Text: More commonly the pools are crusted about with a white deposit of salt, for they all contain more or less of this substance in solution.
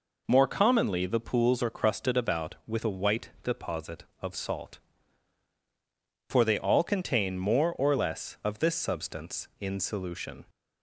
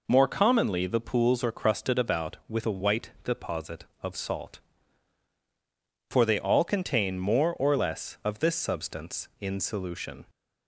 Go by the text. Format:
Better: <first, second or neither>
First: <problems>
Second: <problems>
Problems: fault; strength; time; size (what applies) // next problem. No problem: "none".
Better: neither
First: none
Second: none